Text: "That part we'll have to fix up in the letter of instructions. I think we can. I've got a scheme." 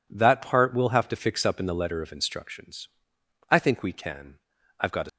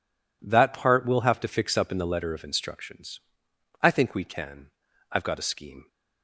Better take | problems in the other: second | stops before "scheme"; at 5.0 s

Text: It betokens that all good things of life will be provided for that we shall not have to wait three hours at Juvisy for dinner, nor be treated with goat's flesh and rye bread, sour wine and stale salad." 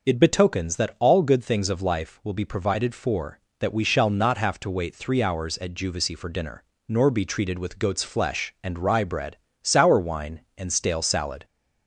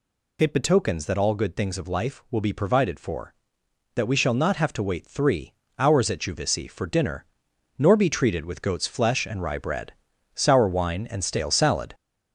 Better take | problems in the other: first | gets louder; noticeable; throughout; 4.5 dB // pauses between "three" and "hours"; slight; at 5.5 s; 0.26 s long

